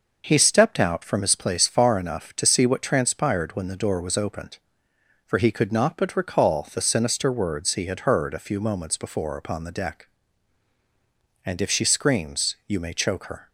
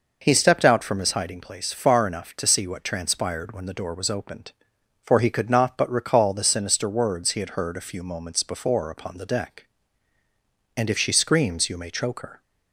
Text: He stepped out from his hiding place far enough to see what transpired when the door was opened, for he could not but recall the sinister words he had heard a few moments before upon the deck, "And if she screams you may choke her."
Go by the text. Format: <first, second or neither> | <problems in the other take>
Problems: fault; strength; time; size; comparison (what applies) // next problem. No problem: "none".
second | skips "hiding"; at 1.3 s